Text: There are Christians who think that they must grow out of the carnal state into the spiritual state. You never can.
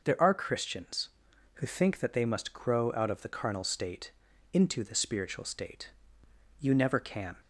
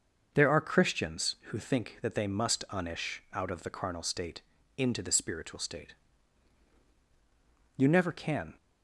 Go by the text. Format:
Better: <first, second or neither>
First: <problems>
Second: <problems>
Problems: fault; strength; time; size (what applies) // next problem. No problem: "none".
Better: first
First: pauses between "state" and "into"; at 4.1 s; 0.42 s long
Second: starts louder than the rest; until 1.3 s; 6.5 dB // says "unish" for "grow"; at 2.6 s // pauses between "state" and "into"; slight; at 4.4 s; 0.36 s long